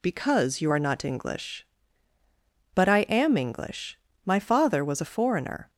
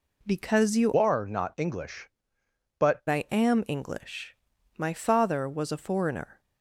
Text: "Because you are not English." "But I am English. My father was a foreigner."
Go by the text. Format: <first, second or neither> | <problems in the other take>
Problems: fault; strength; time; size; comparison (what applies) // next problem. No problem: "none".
first | changes voice from "are" to "But"; from 0.9 to 3.0 s; 2.1 s long